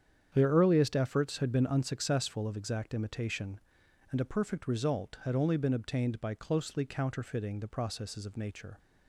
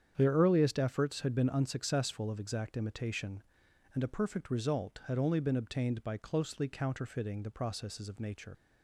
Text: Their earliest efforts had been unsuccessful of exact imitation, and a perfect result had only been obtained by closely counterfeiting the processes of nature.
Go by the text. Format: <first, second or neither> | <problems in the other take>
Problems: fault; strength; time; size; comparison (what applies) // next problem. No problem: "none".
first | starts louder than the rest; strong; until 1.1 s; 8.5 dB; strong in the first // leaves "nature" unfinished; at 8.5 s; 65 ms